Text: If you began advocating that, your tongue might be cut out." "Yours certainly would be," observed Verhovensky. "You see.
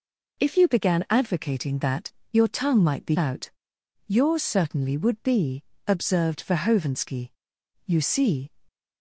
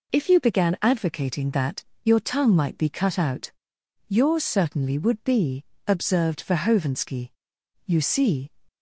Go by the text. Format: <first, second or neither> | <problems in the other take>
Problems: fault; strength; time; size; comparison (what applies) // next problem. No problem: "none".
second | skips "cut"; at 3.1 s